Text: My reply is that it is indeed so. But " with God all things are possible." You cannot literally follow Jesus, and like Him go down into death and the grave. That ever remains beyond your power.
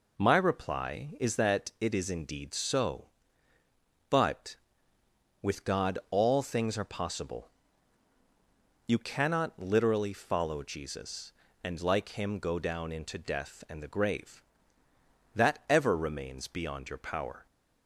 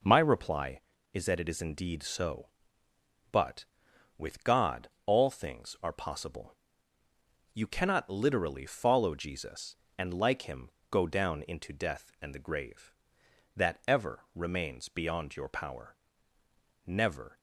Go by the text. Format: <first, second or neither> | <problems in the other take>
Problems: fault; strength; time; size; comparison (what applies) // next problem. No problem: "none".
first | pauses between "God" and "all"; slight; at 4.8 s; 0.18 s long // pauses between "Him" and "go"; slight; at 10.7 s; 0.20 s long // goes on to say "Never"; from 16.8 s on; 0.54 s long